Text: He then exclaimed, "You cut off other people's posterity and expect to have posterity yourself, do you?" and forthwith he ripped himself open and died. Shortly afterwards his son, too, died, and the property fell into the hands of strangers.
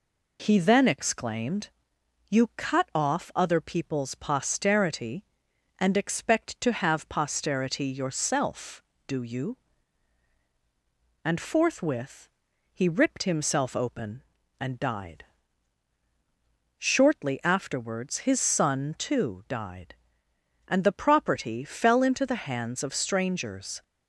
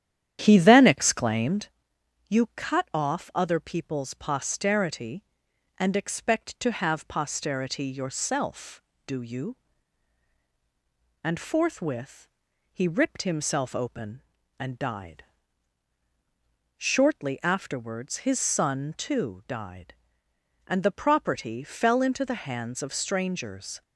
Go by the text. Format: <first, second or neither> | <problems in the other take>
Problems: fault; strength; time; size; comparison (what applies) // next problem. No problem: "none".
first | starts louder than the rest; strong; until 1.7 s; 10 dB // pauses between "forthwith" and "he"; noticeable; at 12.2 s; 0.46 s long; noticeable in the first